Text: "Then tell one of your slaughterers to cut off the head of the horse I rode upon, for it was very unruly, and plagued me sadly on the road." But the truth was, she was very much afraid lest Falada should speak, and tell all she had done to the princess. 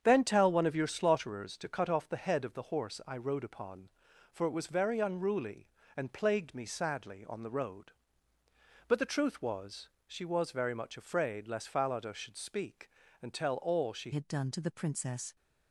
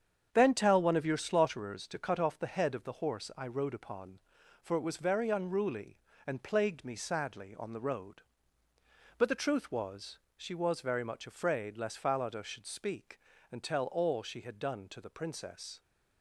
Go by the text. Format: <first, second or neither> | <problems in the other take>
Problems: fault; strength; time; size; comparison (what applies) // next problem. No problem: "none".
second | starts louder than the rest; strong; until 1.0 s; 8 dB; strong in the second // changes voice at "had"; from 14.1 s on; 1.2 s long